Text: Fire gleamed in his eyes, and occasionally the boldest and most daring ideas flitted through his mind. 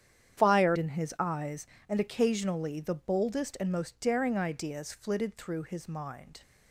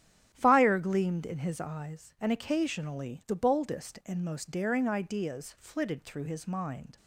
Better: second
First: starts louder than the rest; strong; until 1.4 s; 9.5 dB // skips "gleamed"; at 0.7 s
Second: starts louder than the rest; strong; until 1.3 s; 9.5 dB

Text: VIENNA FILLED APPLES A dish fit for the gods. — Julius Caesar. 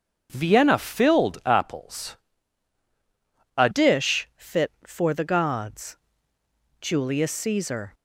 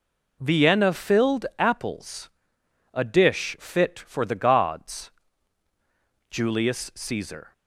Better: second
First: starts louder than the rest; until 1.3 s; 6.5 dB // pauses between "APPLES" and "A"; strong; at 2.1 s; 1.4 s long // changes voice at "dish"; from 3.7 s on; 4.2 s long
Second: pauses between "APPLES" and "A"; noticeable; at 2.3 s; 0.64 s long

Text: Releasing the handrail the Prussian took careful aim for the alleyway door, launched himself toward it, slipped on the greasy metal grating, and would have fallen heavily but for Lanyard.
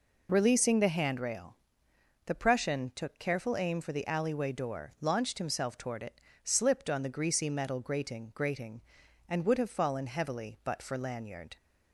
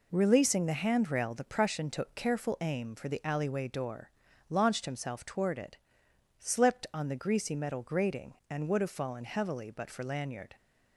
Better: second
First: pauses between "handrail" and "the"; noticeable; at 1.5 s; 0.70 s long // says "grating" twice; at 8.3 s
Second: none

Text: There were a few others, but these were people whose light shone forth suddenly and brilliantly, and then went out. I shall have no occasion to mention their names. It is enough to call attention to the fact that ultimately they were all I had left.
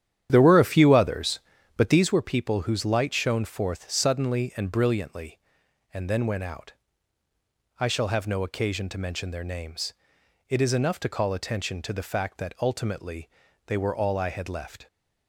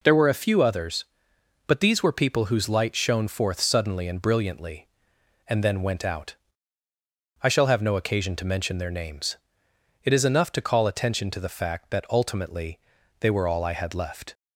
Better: second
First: starts louder than the rest; strong; until 2.2 s; 10 dB // pauses between "ultimately" and "they"; at 13.2 s; 0.38 s long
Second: pauses between "ultimately" and "they"; at 12.7 s; 0.40 s long

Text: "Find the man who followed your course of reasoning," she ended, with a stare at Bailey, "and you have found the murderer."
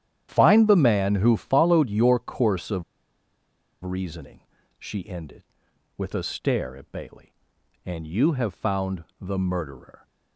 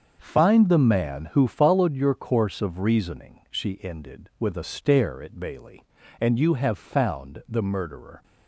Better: second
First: starts louder than the rest; strong; until 1.3 s; 10.5 dB // pauses between "of" and "reasoning"; at 2.8 s; 1.0 s long // pauses between "found" and "the"; slight; at 9.0 s; 0.16 s long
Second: starts louder than the rest; until 1.2 s; 6.5 dB

